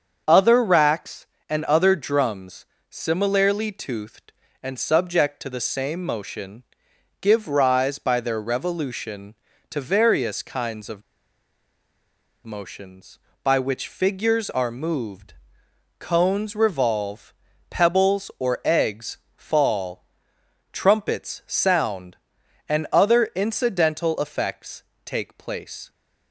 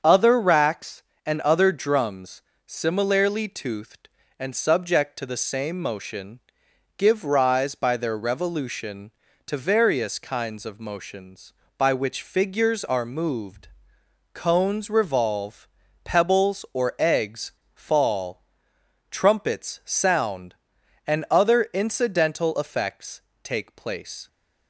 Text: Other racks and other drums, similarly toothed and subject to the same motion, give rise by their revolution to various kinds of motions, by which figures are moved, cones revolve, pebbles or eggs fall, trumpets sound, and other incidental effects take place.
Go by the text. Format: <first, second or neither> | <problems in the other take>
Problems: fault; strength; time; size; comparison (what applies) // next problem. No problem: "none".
second | starts louder than the rest; until 1.5 s; 7 dB; also in the second // pauses between "of" and "motions"; strong; at 11.0 s; 1.4 s long // pauses between "eggs" and "fall"; slight; at 19.1 s; 0.18 s long; slight in the second // pauses between "effects" and "take"; slight; at 24.8 s; 0.20 s long; slight in the second